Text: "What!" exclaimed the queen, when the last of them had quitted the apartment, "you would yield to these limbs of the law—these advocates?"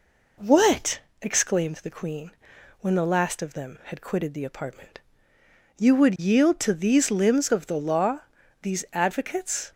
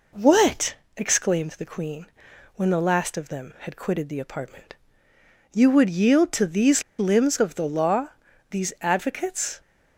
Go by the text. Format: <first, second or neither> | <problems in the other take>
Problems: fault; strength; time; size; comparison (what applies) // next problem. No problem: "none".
first | pauses between "these" and "limbs"; slight; at 6.8 s; 0.17 s long